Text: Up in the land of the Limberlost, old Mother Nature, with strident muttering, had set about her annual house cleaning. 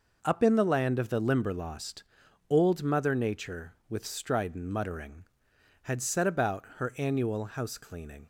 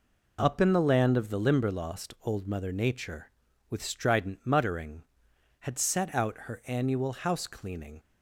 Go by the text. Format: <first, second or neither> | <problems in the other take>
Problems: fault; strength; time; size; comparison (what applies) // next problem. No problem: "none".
first | says "out" for "about"; at 6.1 s